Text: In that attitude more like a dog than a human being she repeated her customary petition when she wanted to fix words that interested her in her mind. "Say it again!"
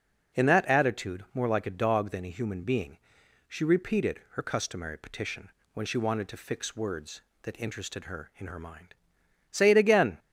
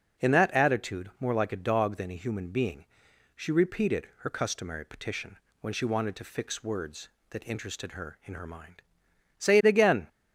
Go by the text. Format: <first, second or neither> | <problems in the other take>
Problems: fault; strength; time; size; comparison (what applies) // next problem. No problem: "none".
neither | pauses between "being" and "she"; noticeable; the same in both // pauses between "petition" and "when"; slight; the same in both